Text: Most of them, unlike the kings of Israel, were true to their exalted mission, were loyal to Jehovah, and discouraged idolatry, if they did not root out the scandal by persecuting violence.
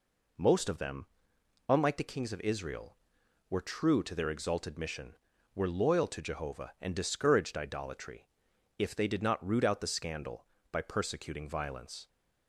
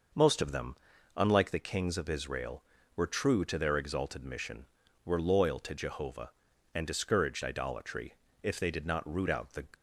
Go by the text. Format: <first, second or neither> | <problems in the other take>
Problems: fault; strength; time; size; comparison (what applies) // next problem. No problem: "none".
first | stops before "scandal by persecuting violence"; at 9.7 s